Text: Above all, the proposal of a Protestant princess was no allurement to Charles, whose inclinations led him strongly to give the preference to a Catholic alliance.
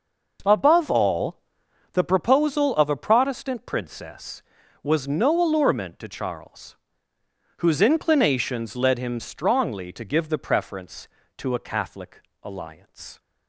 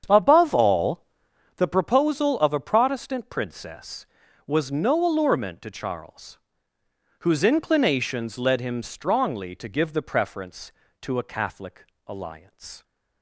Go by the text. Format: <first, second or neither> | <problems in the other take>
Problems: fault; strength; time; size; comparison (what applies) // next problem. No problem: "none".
first | starts louder than the rest; strong; until 1.5 s; 8 dB // pauses between "Catholic" and "alliance"; slight; at 11.8 s; 0.20 s long; slight in the first